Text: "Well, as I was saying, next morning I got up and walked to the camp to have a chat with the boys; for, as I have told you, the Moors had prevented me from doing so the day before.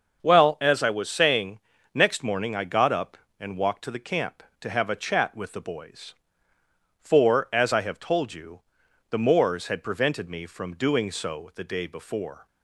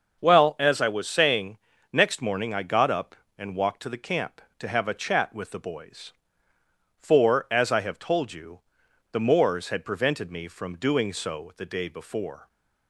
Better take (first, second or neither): neither